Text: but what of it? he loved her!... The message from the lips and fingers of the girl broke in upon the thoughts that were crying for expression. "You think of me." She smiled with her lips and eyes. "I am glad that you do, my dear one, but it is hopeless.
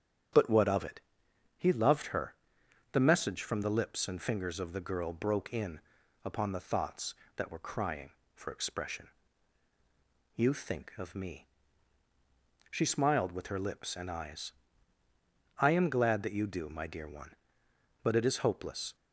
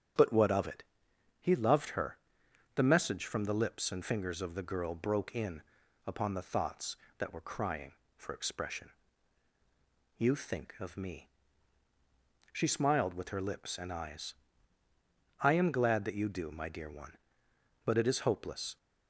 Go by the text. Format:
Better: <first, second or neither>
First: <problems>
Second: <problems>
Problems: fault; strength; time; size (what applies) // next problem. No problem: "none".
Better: neither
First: starts louder than the rest; strong; until 1.9 s; 8.5 dB // pauses between "in" and "upon"; noticeable; at 5.7 s; 0.46 s long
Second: starts louder than the rest; strong; until 1.7 s; 8.5 dB // pauses between "in" and "upon"; noticeable; at 5.6 s; 0.46 s long